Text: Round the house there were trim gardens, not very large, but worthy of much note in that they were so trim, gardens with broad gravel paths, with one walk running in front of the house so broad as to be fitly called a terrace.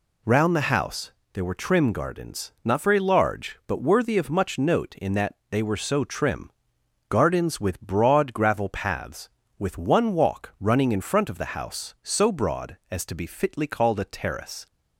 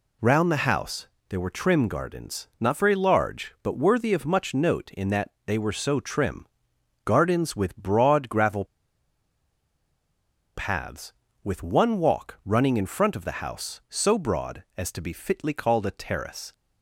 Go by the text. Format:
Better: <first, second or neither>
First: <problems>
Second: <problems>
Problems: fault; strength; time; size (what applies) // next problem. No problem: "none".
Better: first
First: pauses between "house" and "there"; slight; at 1.1 s; 0.22 s long // pauses between "that" and "they"; slight; at 5.3 s; 0.16 s long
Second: pauses between "house" and "there"; slight; at 1.0 s; 0.22 s long // pauses between "that" and "they"; slight; at 5.2 s; 0.16 s long // pauses between "gravel" and "paths"; strong; at 8.6 s; 1.9 s long